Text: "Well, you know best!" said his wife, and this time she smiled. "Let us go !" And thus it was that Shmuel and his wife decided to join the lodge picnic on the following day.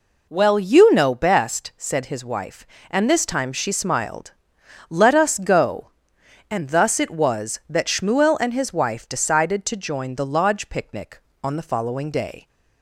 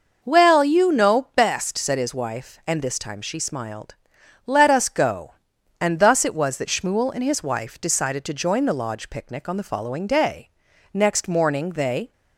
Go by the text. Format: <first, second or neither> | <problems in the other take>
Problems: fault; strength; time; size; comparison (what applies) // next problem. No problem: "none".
first | goes on to say "Next morning they"; noticeable; from 10.9 s on; 1.1 s long